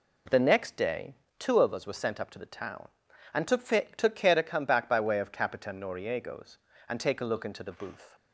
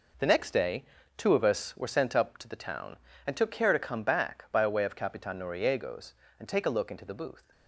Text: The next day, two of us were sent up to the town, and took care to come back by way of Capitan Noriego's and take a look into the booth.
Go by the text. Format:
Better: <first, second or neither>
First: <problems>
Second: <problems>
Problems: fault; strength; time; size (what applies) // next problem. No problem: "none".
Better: second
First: says "took" twice; at 3.9 s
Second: none